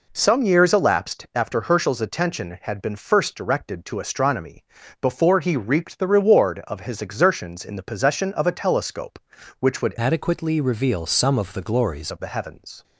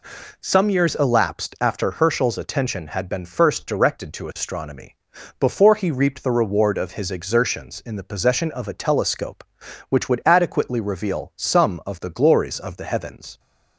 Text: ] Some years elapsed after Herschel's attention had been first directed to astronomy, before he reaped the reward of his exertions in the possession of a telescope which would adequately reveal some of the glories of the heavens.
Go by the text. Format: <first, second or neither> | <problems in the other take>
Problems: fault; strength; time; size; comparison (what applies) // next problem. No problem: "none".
second | changes voice from "adequately" to "glories"; from 9.9 to 12.1 s; 2.2 s long